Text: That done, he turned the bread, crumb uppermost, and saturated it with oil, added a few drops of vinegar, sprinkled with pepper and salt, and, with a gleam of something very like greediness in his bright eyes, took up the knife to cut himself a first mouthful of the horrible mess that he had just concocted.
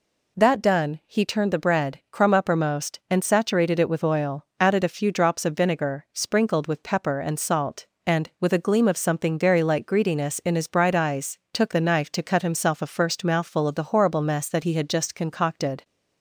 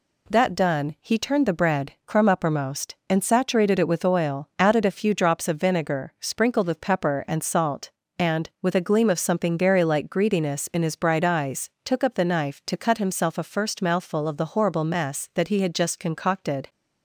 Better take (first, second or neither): second